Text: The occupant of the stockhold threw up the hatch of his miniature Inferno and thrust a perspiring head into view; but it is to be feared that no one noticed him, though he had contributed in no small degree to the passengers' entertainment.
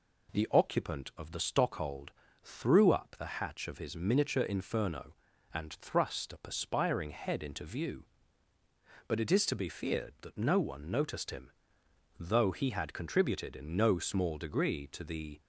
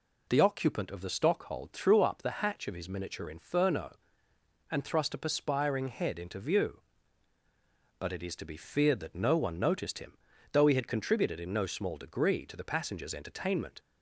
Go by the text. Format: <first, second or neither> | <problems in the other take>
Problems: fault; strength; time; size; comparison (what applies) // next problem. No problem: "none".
second | pauses between "stockhold" and "threw"; slight; at 2.1 s; 0.34 s long // stops before "passengers entertainment"; at 15.4 s